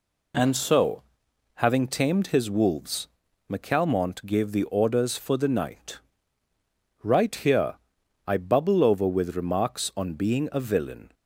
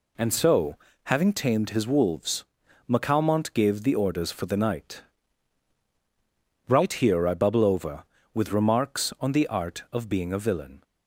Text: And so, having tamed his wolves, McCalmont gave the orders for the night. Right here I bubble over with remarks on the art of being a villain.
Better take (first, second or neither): second